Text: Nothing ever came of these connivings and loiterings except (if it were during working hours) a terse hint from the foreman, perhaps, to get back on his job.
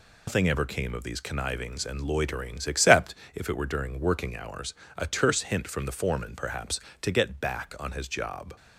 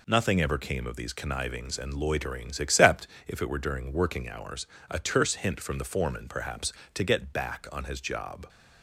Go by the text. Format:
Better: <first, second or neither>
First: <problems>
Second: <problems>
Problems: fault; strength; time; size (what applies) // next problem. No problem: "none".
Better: second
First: loses the start of "Nothing"; at 0.2 s; 140 ms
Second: none